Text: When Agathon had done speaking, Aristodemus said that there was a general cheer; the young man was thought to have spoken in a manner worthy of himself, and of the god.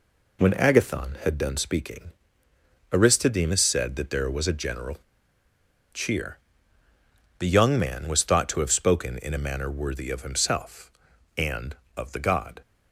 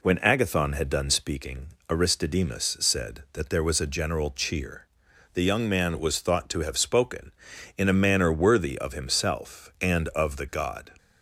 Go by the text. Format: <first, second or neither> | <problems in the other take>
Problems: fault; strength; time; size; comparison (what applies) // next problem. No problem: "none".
second | pauses between "general" and "cheer"; noticeable; at 4.9 s; 0.97 s long